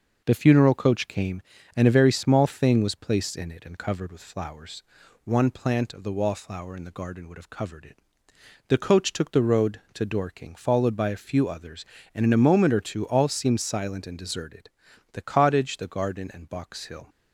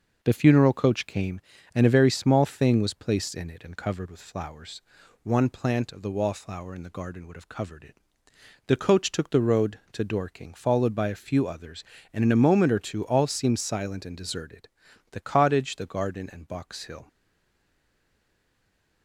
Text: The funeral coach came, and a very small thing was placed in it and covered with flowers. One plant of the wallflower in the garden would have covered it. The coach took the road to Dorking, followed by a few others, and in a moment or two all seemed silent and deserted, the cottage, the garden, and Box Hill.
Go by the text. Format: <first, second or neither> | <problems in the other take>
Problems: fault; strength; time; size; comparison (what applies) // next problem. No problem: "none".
first | stays silent after the last word; noticeable; from 17.0 s on; 2.0 s long